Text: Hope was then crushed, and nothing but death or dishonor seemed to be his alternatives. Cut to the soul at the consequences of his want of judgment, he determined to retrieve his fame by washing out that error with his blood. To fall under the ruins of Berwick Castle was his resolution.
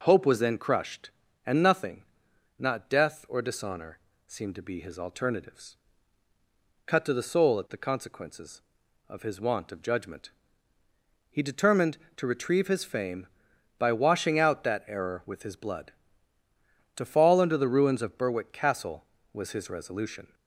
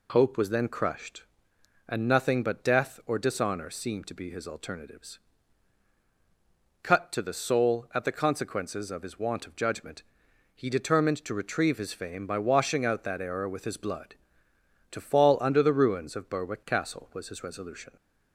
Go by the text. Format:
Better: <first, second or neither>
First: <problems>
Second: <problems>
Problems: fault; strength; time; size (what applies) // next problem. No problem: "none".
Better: second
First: says "not" for "but"; at 2.5 s // pauses between "dishonor" and "seemed"; slight; at 3.9 s; 0.26 s long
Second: none